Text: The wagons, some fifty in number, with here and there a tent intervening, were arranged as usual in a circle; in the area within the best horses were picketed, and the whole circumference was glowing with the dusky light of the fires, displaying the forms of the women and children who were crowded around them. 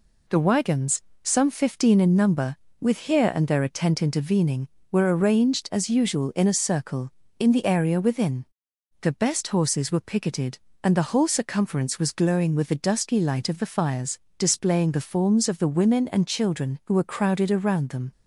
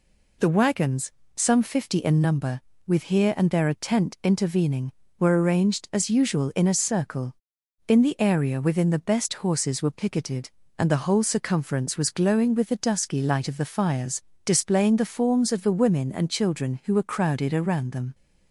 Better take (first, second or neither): second